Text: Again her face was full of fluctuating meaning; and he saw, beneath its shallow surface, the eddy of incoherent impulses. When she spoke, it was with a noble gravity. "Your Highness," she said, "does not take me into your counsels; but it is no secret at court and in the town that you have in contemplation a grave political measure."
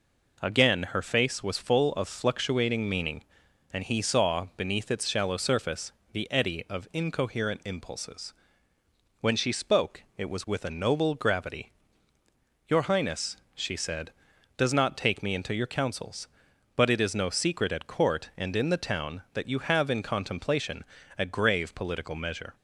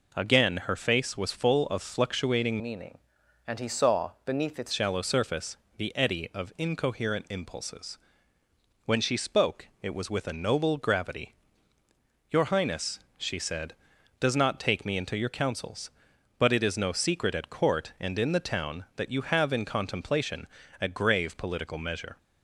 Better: first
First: pauses between "contemplation" and "a"; slight; at 20.8 s; 0.36 s long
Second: changes voice from "meaning" to "its"; from 2.6 to 4.7 s; 2.1 s long // pauses between "contemplation" and "a"; slight; at 20.4 s; 0.36 s long

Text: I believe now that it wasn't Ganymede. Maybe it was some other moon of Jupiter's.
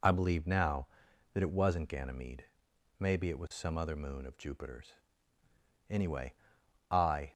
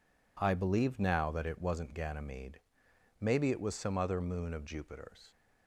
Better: second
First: goes on to say "Anyway I"; from 5.8 s on; 1.4 s long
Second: none

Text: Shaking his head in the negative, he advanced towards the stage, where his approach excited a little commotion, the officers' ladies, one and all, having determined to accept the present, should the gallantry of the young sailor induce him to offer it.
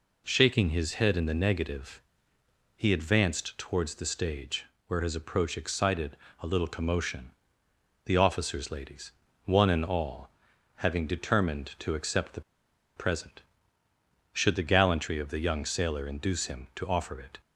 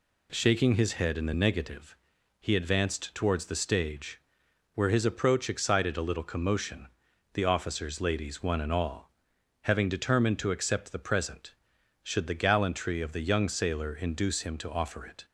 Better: second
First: pauses between "excited" and "a"; slight; at 6.1 s; 0.24 s long // pauses between "the" and "present"; noticeable; at 12.4 s; 0.56 s long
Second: none

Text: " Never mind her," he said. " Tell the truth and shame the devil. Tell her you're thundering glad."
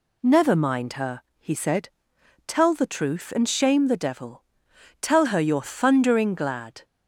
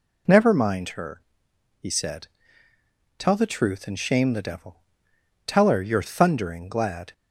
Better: second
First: changes voice at "Never"; from 0.2 s on; 6.6 s long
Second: none

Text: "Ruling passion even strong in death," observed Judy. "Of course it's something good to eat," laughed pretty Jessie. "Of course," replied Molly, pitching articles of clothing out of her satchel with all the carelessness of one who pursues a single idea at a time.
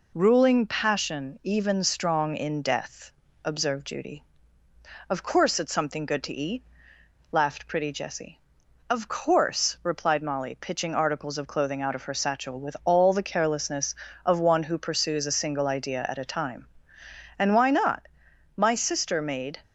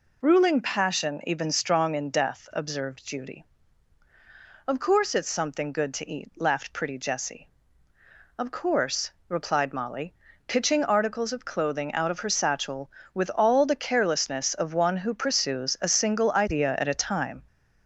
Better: second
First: goes on to say "And why not My sister made"; strong; from 17.3 s on; 2.2 s long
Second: none

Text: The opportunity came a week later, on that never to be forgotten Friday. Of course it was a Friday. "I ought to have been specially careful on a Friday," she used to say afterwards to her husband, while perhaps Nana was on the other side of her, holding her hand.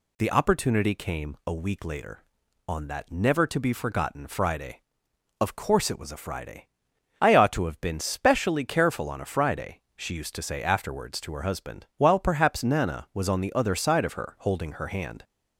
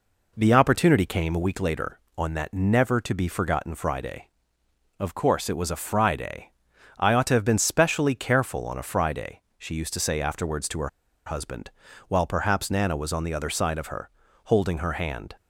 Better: first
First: none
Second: pauses between "her" and "husband"; at 10.8 s; 0.38 s long

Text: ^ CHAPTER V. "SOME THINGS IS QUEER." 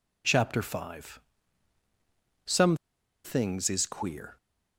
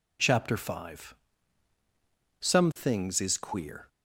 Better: second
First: pauses between "SOME" and "THINGS"; noticeable; at 2.7 s; 0.48 s long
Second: none

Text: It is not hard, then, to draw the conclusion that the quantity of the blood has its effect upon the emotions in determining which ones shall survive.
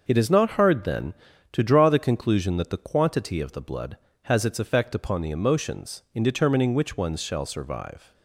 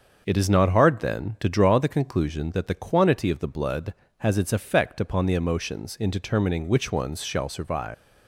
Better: first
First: starts louder than the rest; until 1.0 s; 6.5 dB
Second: starts louder than the rest; until 1.2 s; 6.5 dB // leaves "survive" unfinished; at 7.9 s; 230 ms

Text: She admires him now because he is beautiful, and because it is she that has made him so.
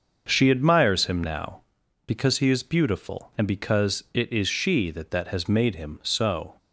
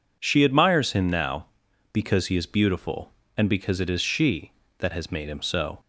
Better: second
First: starts louder than the rest; until 1.2 s; 6.5 dB // says "that" twice; at 5.1 s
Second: none

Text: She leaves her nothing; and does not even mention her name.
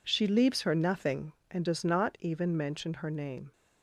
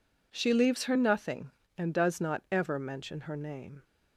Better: first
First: none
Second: says "ever" for "even"; at 2.4 s

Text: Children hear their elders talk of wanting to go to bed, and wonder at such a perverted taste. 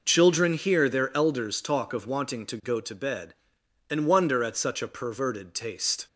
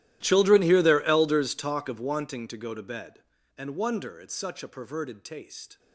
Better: first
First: none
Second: gets quieter; strong; throughout; 23.5 dB

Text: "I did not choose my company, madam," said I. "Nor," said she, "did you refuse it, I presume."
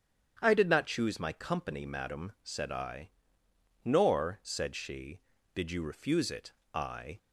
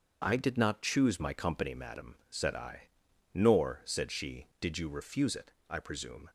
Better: second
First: starts louder than the rest; strong; until 1.4 s; 9 dB // stops before "presume"; at 7.1 s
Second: starts louder than the rest; until 1.2 s; 6.5 dB

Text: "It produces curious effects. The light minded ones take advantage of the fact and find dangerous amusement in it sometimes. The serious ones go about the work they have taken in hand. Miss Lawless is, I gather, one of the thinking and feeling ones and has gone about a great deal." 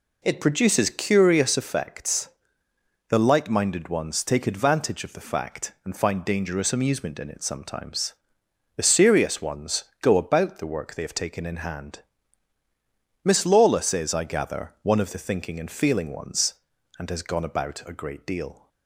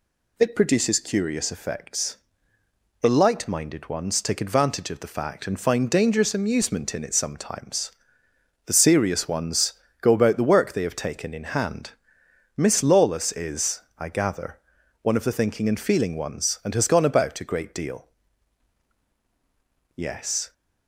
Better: first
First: pauses between "ones" and "go"; slight; at 9.8 s; 0.16 s long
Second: pauses between "ones" and "go"; slight; at 9.7 s; 0.26 s long // goes on to say "Yes"; from 19.9 s on; 0.58 s long

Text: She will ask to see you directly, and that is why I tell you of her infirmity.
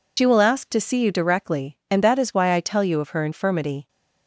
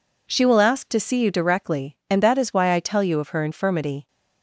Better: second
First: loses the start of "She"; at 0.1 s; 75 ms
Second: none

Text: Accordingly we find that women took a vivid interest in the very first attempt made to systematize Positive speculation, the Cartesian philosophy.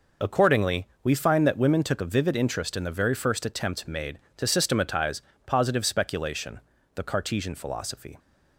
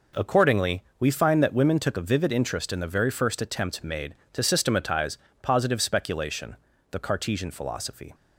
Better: second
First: loses the start of "Accordingly"; at 0.2 s; 35 ms // pauses between "Accordingly" and "we"; slight; at 0.8 s; 0.16 s long // pauses between "systematize" and "Positive"; slight; at 5.2 s; 0.24 s long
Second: pauses between "Accordingly" and "we"; slight; at 0.8 s; 0.16 s long // pauses between "systematize" and "Positive"; slight; at 5.1 s; 0.24 s long

